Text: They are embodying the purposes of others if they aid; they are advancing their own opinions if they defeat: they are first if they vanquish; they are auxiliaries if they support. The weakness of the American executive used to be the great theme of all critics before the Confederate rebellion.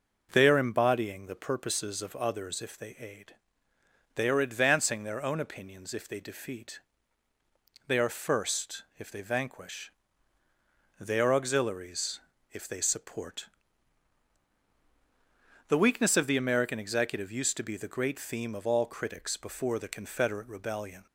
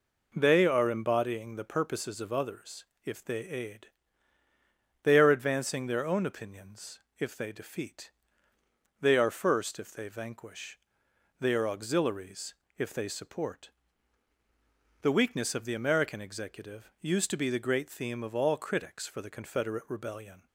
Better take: first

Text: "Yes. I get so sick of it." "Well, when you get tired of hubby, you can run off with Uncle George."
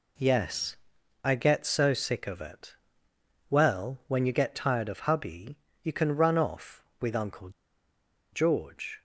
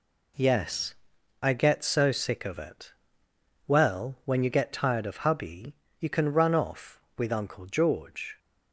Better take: second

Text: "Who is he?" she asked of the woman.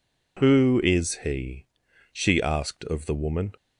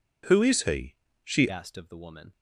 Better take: first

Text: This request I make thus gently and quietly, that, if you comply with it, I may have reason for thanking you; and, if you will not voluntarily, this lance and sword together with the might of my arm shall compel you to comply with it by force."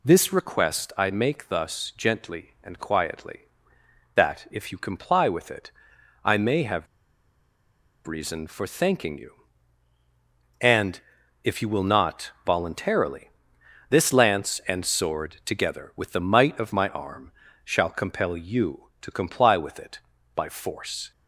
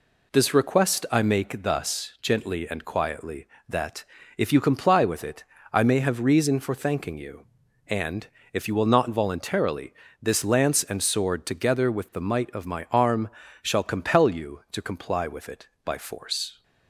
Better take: second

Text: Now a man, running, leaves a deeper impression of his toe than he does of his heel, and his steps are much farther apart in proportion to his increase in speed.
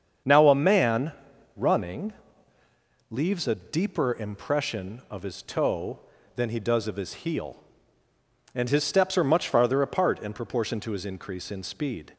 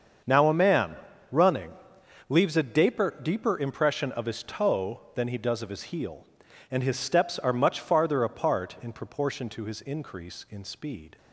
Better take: first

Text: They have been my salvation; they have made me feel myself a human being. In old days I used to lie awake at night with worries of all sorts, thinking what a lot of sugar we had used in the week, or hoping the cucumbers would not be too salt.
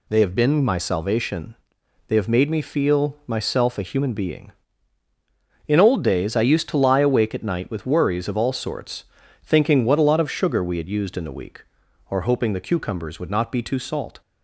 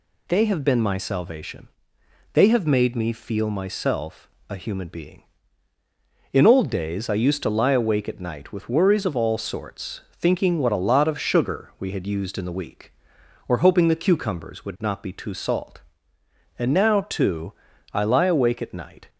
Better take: first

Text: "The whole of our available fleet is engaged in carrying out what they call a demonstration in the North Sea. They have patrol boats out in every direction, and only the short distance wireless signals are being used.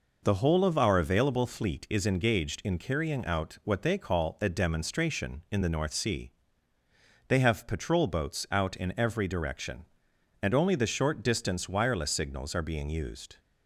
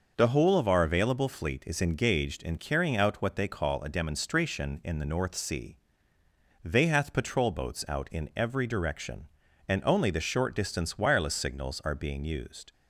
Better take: first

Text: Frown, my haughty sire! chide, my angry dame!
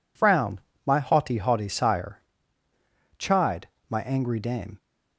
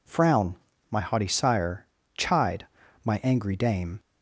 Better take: second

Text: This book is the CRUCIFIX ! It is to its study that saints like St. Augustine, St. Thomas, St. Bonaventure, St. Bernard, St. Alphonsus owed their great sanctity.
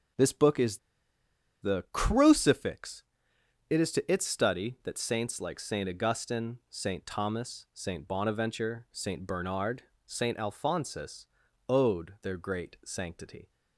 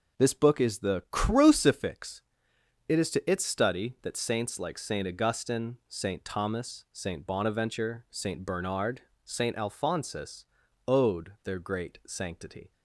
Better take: second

